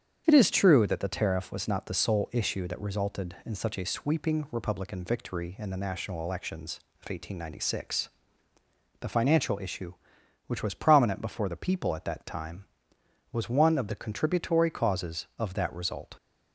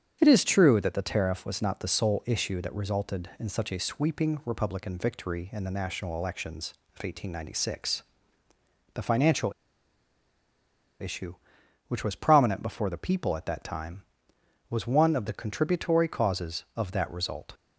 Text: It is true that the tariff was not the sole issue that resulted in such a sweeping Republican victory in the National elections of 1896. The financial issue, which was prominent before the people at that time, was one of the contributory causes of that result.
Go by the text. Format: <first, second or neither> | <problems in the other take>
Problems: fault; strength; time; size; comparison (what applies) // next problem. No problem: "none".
first | starts louder than the rest; strong; until 1.2 s; 8 dB; strong in the first // pauses between "financial" and "issue"; strong; at 9.5 s; 1.4 s long